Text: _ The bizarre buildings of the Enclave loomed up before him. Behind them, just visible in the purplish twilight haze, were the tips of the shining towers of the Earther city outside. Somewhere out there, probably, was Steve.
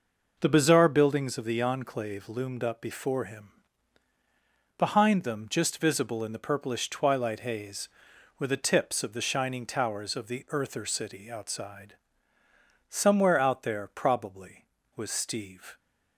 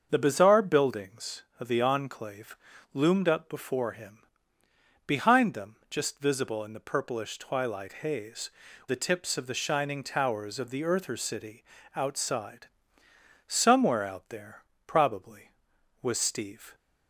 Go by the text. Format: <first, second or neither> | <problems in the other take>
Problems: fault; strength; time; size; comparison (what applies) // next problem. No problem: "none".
first | starts louder than the rest; until 1.1 s; 6.5 dB // pauses between "Enclave" and "loomed"; slight; at 2.5 s; 0.36 s long // skips "were"; at 8.6 s // pauses between "city" and "outside"; slight; at 11.6 s; 0.32 s long